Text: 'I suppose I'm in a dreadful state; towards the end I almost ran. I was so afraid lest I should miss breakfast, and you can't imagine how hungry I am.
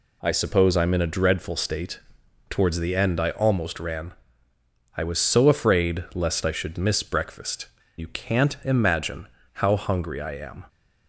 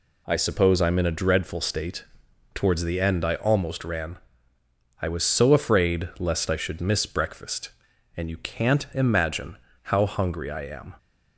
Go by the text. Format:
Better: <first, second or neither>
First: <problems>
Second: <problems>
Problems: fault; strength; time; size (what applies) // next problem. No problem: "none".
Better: second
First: skips "and"; at 7.8 s // pauses between "imagine" and "how"; slight; at 9.2 s; 0.28 s long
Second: pauses between "imagine" and "how"; slight; at 9.5 s; 0.28 s long